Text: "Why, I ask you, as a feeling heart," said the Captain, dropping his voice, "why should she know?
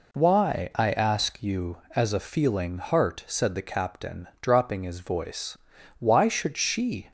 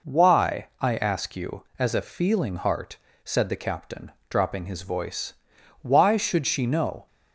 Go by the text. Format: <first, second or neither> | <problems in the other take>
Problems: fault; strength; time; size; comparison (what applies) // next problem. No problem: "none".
second | stops before "know"; at 7.0 s